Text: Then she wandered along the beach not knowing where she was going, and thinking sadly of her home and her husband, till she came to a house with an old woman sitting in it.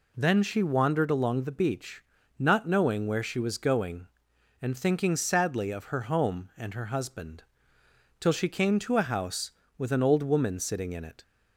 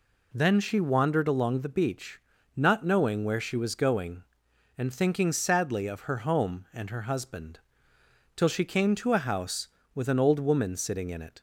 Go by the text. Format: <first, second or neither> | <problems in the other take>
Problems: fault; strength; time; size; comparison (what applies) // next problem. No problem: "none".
neither | pauses between "beach" and "not"; slight; the same in both